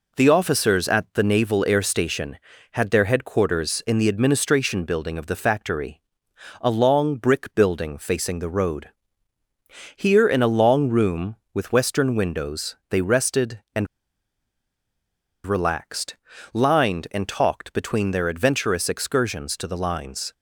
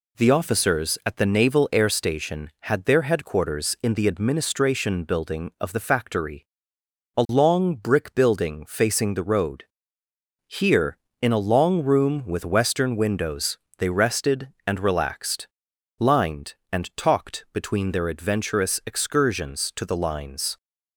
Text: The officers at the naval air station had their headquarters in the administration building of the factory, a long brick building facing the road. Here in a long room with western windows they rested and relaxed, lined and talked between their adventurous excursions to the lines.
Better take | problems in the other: second | pauses between "windows" and "they"; slight; at 12.7 s; 0.16 s long; slight in the second // pauses between "and" and "relaxed"; strong; at 13.8 s; 1.5 s long

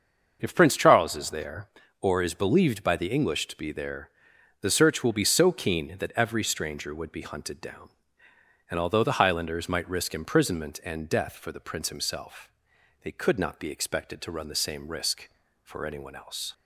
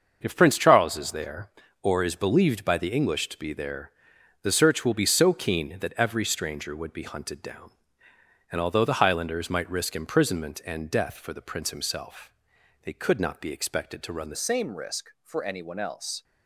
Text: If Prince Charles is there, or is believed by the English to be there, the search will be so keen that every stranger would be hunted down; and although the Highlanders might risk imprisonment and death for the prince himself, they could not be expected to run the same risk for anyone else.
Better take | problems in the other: first | starts louder than the rest; until 1.2 s; 6.5 dB; also in the first // changes voice at "same"; from 14.3 s on; 1.9 s long

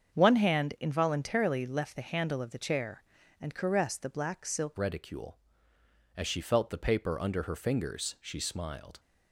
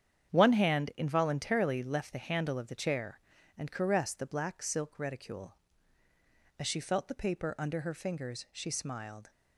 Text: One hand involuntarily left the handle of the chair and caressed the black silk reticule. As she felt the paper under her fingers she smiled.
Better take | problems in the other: second | starts louder than the rest; strong; until 1.1 s; 7.5 dB; strong in the second // changes voice at "reticule"; from 4.7 s on; 4.2 s long

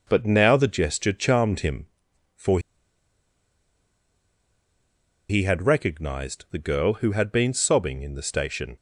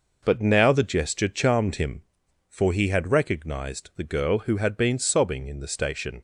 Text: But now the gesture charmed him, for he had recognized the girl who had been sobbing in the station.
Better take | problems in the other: second | pauses between "for" and "he"; strong; at 2.5 s; 2.6 s long

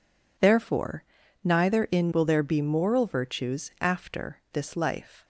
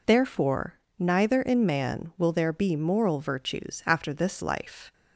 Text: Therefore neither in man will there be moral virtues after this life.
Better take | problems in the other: second | pauses between "Therefore" and "neither"; at 1.0 s; 0.40 s long; slight in the second // skips "man"; at 2.1 s

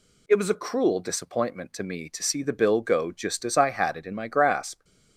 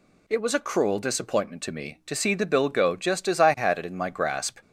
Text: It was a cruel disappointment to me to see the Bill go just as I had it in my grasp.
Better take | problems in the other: neither | none

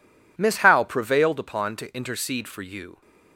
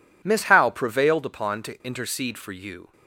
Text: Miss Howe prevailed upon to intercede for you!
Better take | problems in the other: neither | none

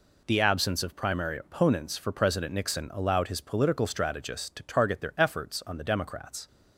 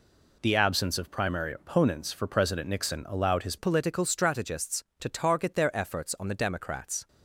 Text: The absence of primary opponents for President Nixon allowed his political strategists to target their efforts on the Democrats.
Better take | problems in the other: first | changes voice at "political"; from 3.5 s on; 3.5 s long

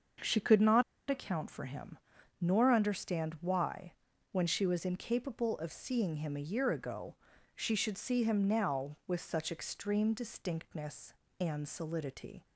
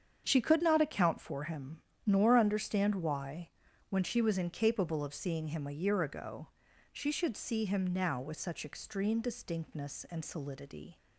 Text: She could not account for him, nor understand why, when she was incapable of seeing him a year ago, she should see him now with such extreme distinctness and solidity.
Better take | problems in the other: second | starts louder than the rest; until 1.4 s; 6.5 dB; strong in the second // pauses between "not" and "account"; slight; at 0.8 s; 0.27 s long

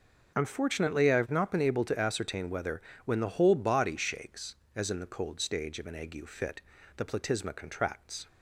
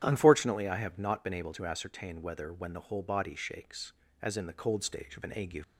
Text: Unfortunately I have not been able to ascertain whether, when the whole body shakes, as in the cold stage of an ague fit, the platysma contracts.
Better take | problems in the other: first | starts louder than the rest; strong; until 1.0 s; 9.5 dB // stops before "fit the platysma contracts"; at 5.6 s

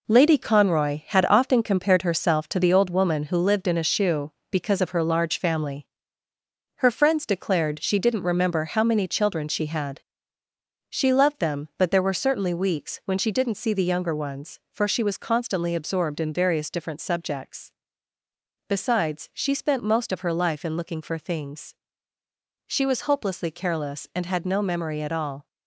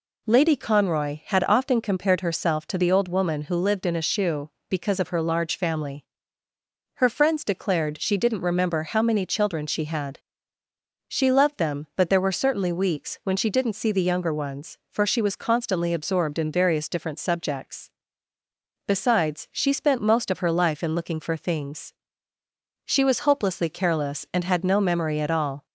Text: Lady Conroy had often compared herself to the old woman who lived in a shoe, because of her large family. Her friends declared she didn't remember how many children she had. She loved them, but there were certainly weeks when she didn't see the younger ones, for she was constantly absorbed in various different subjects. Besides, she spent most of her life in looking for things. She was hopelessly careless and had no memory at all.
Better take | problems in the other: second | gets quieter; strong; throughout; 7 dB

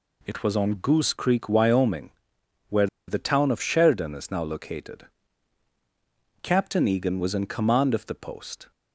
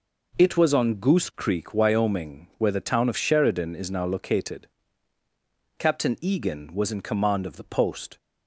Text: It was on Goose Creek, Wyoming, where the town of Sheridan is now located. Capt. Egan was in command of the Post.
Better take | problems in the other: second | pauses between "where" and "the"; slight; at 2.8 s; 0.21 s long

